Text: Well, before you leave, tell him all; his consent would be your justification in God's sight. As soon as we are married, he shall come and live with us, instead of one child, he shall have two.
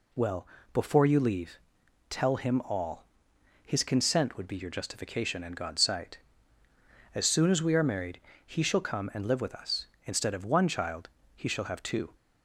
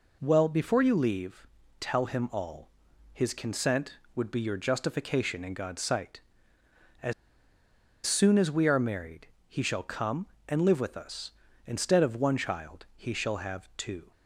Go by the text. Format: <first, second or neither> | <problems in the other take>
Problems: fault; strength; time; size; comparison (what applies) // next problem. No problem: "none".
first | pauses between "As" and "soon"; noticeable; at 7.1 s; 0.93 s long